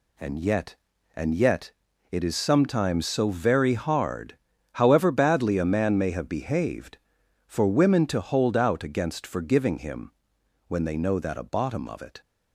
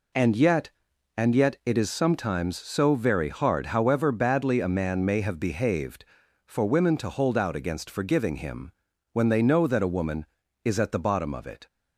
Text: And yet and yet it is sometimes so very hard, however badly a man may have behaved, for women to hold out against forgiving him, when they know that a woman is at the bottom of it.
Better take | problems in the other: second | pauses between "yet" and "it"; at 1.7 s; 0.40 s long // skips "woman is at the"; at 11.4 s

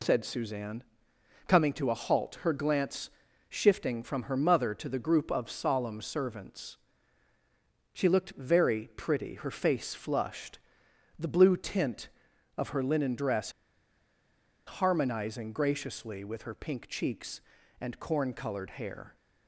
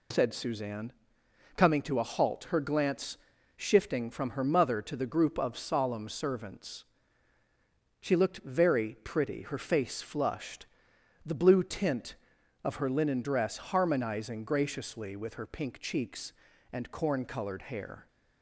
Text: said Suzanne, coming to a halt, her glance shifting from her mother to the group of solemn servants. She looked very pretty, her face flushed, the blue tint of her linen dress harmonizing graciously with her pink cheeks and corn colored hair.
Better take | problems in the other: second | pauses between "glance" and "shifting"; at 3.0 s; 0.40 s long; also in the second // pauses between "dress" and "harmonizing"; at 13.5 s; 1.1 s long

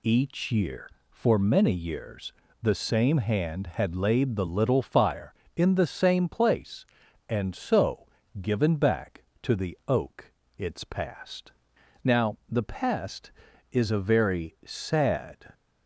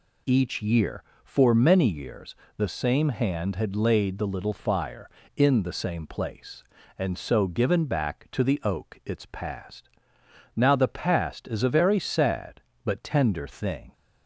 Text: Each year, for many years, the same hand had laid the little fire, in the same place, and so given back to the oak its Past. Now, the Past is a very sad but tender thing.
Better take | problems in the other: second | pauses between "so" and "given"; slight; at 8.0 s; 0.36 s long // pauses between "oak" and "its"; slight; at 10.3 s; 0.24 s long // stops before "but tender thing"; at 15.5 s

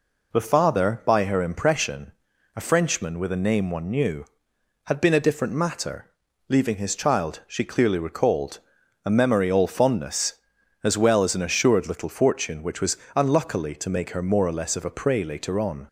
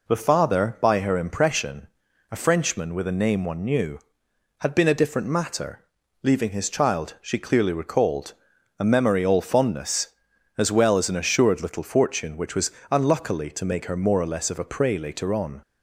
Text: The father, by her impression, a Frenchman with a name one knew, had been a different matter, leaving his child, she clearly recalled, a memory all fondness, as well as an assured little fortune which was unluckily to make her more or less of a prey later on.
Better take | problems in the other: neither | pauses between "was" and "unluckily"; slight; the same in both

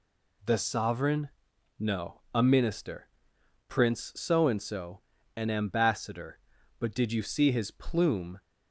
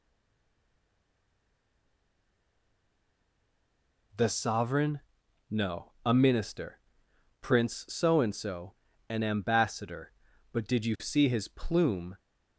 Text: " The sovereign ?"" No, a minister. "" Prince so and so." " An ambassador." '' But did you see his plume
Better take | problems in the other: first | stays silent before the first word; strong; until 4.1 s; 4.1 s long

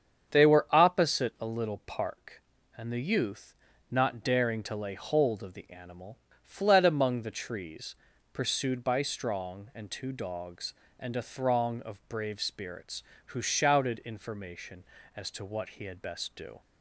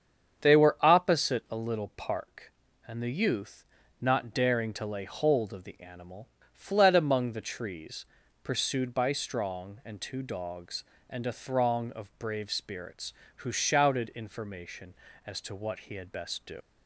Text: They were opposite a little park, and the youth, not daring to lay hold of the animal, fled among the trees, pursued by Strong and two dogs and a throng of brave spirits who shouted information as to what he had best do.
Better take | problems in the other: first | starts louder than the rest; strong; until 1.5 s; 7.5 dB; strong in the first // leaves "do" unfinished; at 16.6 s; 95 ms

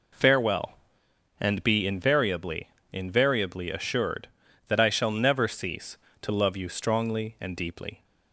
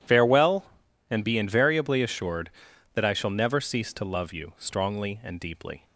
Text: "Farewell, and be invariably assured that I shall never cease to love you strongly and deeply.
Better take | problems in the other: second | says "invariably" twice; at 2.9 s

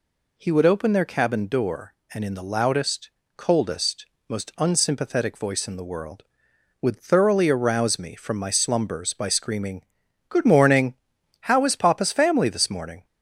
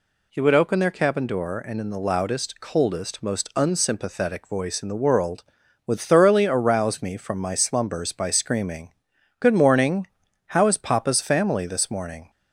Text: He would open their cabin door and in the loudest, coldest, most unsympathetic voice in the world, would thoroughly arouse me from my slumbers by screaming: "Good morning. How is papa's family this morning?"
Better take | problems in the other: neither | none

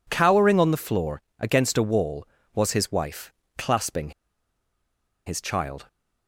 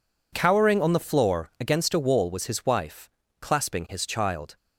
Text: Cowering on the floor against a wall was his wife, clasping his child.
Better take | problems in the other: second | pauses between "floor" and "against"; slight; at 1.2 s; 0.18 s long // pauses between "clasping" and "his"; at 4.1 s; 1.1 s long

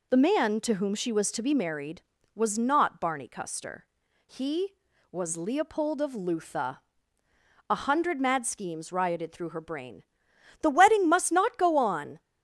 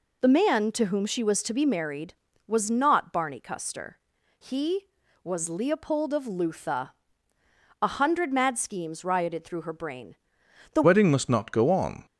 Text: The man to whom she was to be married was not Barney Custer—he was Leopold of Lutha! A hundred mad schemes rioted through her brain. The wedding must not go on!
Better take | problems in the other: first | changes voice at "wedding"; from 10.8 s on; 1.2 s long

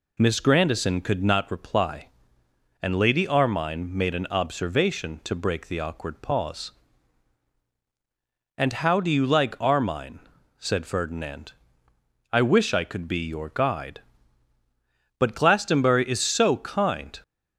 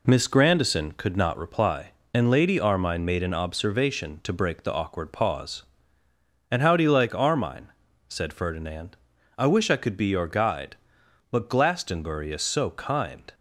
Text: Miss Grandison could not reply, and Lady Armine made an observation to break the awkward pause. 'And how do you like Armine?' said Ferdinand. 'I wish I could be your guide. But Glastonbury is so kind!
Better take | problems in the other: first | gets quieter; noticeable; throughout; 5 dB

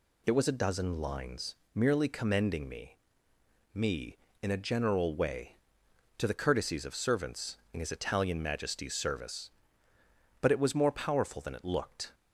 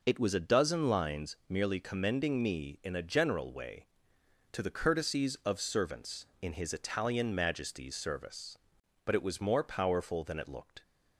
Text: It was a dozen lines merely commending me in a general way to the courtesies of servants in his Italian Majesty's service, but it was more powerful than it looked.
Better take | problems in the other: second | pauses between "lines" and "merely"; slight; at 1.5 s; 0.18 s long // says "me" twice; at 3.7 s

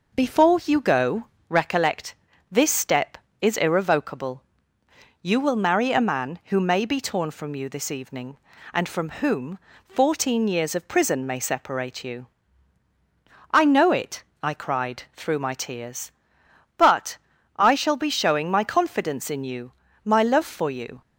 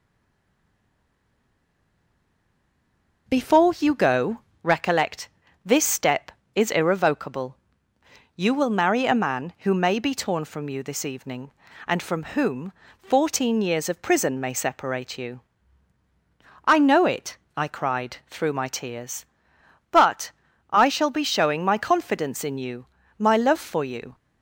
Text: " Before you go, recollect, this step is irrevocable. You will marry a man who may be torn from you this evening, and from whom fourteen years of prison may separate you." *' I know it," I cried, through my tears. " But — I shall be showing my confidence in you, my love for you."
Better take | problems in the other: first | stays silent before the first word; strong; until 3.2 s; 3.2 s long // pauses between "from" and "whom"; slight; at 12.2 s; 0.16 s long; slight in the first // pauses between "whom" and "fourteen"; slight; at 12.7 s; 0.30 s long; slight in the first

